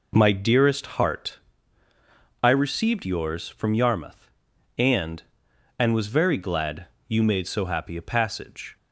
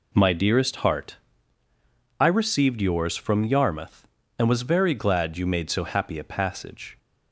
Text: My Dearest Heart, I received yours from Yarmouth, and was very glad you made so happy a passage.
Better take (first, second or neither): second